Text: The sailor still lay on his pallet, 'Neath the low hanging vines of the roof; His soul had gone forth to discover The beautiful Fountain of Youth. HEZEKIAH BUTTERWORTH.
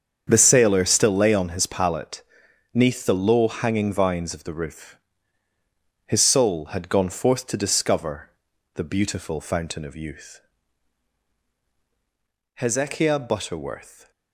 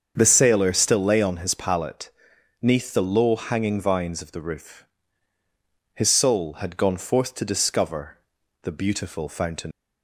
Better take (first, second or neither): first